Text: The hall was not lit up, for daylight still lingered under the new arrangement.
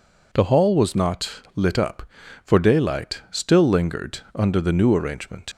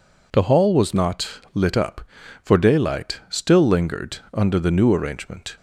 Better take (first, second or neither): second